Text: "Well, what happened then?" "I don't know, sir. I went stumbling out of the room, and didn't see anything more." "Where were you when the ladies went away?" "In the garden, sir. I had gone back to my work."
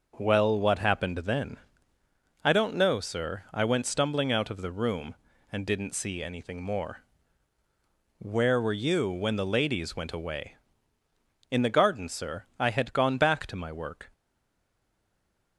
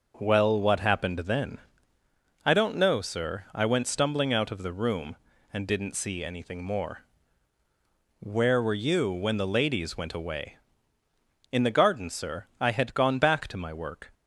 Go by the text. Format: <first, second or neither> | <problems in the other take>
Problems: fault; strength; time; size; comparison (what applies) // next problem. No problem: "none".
second | stays silent after the last word; noticeable; from 14.1 s on; 1.4 s long